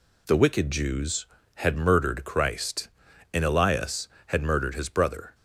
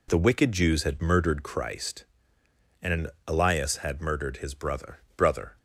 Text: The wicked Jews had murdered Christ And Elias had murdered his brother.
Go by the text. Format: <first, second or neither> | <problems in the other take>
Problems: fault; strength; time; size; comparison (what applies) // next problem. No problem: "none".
first | pauses between "And" and "Elias"; slight; at 3.1 s; 0.16 s long // says "brother" twice; at 5.1 s